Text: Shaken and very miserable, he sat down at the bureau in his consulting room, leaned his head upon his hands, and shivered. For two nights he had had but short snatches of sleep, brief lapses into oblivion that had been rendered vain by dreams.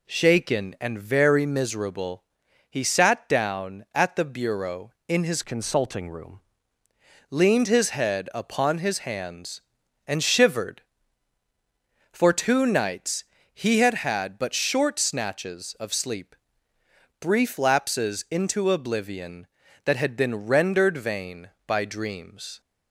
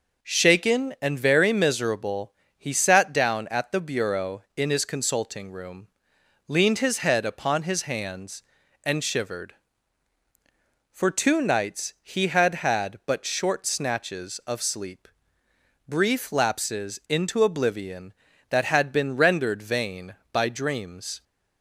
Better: second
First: changes voice from "consulting" to "room"; from 5.4 to 6.3 s; 0.9 s long // pauses between "nights" and "he"; slight; at 13.2 s; 0.32 s long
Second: none

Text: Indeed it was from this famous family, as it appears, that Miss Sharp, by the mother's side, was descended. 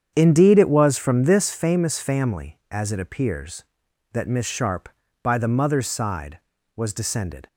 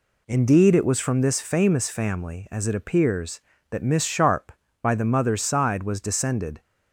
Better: second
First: starts louder than the rest; strong; until 1.6 s; 8 dB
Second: none

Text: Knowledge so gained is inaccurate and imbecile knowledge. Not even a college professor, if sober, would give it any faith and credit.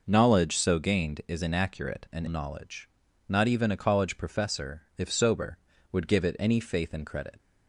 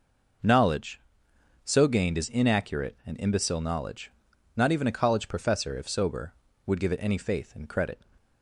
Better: second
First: skips "imbecile"; at 2.2 s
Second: none

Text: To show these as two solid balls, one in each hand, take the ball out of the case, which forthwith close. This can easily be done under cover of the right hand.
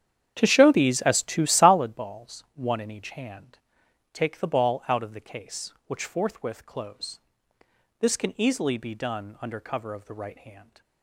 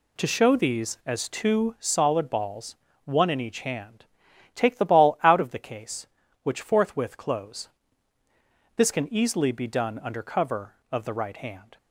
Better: second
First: starts louder than the rest; strong; until 1.9 s; 9 dB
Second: none

